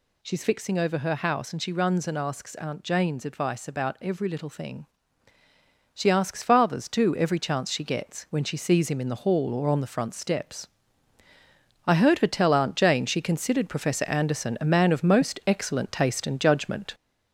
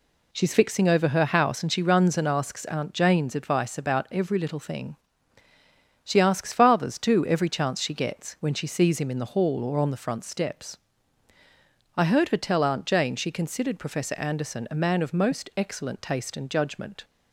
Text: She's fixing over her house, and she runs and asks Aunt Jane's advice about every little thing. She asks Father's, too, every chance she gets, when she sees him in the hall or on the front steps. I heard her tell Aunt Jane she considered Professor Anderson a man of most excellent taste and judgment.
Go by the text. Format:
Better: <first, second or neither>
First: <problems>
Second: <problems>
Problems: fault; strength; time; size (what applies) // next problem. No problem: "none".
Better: second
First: gets louder; noticeable; throughout; 4 dB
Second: none